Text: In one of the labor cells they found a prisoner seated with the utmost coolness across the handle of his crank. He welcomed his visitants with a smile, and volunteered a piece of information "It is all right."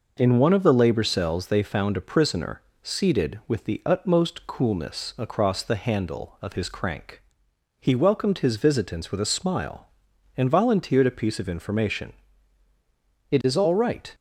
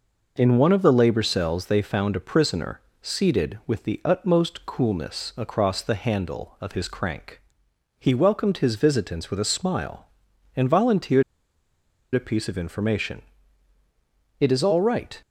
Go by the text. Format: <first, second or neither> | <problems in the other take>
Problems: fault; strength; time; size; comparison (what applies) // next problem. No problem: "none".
first | pauses between "prisoner" and "seated"; slight; at 2.7 s; 0.22 s long; slight in the first // pauses between "volunteered" and "a"; noticeable; at 11.2 s; 0.92 s long // pauses between "information" and "It"; at 13.2 s; 1.1 s long; also in the first